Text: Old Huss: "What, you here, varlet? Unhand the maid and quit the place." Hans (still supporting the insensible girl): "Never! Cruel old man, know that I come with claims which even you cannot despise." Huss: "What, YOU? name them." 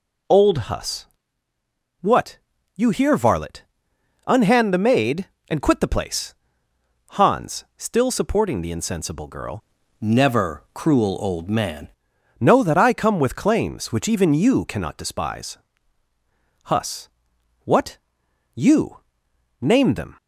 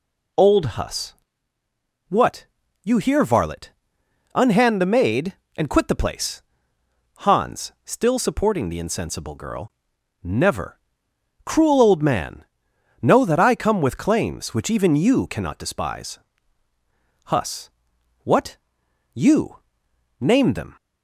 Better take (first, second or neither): second